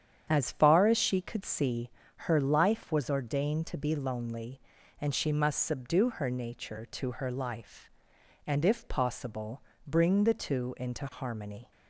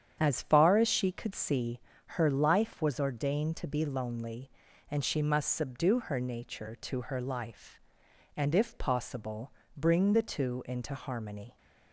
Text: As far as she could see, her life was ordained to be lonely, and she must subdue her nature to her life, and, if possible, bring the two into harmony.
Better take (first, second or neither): neither